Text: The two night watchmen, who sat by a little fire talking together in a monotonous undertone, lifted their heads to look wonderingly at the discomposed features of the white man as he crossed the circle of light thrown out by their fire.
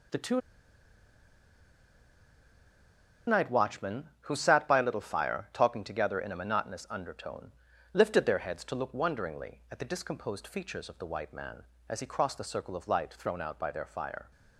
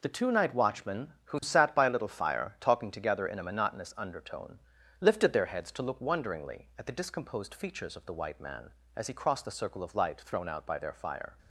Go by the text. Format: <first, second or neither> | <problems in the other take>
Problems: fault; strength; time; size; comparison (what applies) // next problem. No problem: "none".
second | pauses between "two" and "night"; strong; at 0.3 s; 2.8 s long